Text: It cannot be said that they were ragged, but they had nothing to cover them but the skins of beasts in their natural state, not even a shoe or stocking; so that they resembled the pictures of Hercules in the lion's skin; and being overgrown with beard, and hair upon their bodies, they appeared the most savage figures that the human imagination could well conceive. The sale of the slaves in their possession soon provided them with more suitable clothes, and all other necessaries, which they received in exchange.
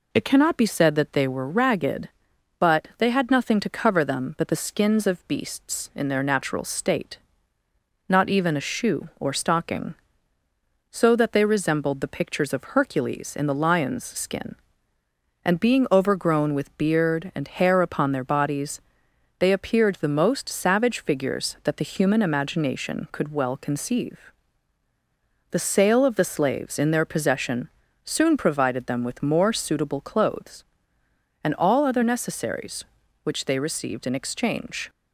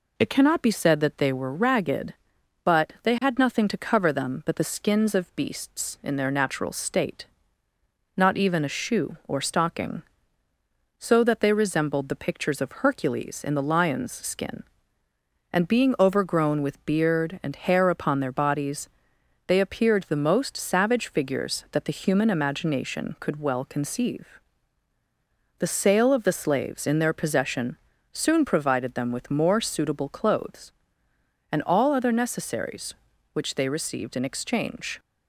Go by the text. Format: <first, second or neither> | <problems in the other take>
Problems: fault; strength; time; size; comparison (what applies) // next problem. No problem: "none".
neither | pauses between "possession" and "soon"; slight; the same in both